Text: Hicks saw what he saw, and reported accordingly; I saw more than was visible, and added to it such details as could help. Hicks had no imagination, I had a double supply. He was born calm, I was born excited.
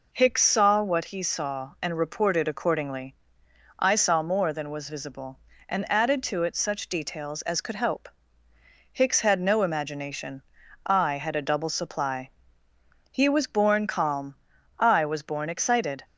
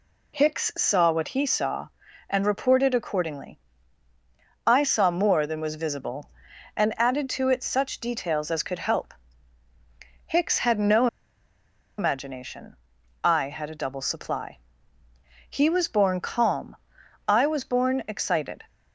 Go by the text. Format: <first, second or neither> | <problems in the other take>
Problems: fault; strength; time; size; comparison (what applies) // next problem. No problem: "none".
first | pauses between "no" and "imagination"; noticeable; at 11.0 s; 0.92 s long